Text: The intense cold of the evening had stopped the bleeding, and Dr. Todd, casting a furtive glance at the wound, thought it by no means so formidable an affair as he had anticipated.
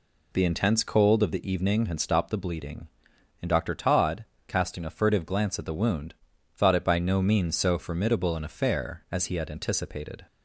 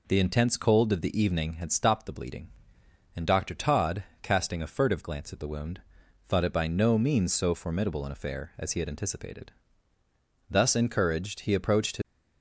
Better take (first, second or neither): first